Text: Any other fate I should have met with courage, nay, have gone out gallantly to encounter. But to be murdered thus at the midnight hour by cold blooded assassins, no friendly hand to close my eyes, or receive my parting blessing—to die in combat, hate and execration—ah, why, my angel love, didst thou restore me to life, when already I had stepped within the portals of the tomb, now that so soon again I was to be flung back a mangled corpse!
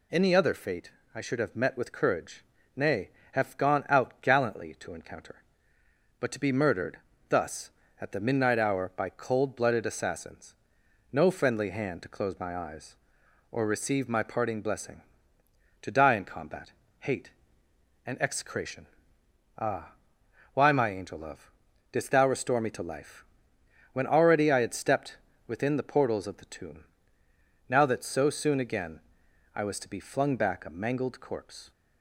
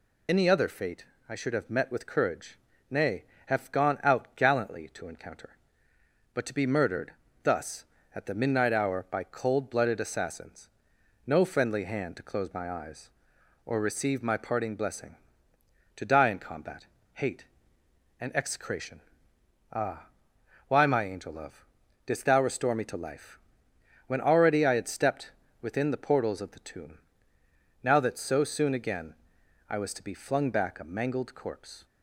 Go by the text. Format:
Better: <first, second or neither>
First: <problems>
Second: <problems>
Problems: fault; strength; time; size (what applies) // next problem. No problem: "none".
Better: first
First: pauses between "fate" and "I"; slight; at 0.9 s; 0.22 s long // pauses between "murdered" and "thus"; slight; at 6.9 s; 0.32 s long // pauses between "stepped" and "within"; slight; at 25.1 s; 0.30 s long // pauses between "again" and "I"; noticeable; at 29.0 s; 0.52 s long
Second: loses the start of "Any"; at 0.2 s; 35 ms // pauses between "fate" and "I"; slight; at 1.0 s; 0.22 s long // pauses between "murdered" and "thus"; slight; at 7.1 s; 0.32 s long // pauses between "stepped" and "within"; slight; at 25.3 s; 0.30 s long // pauses between "again" and "I"; noticeable; at 29.1 s; 0.52 s long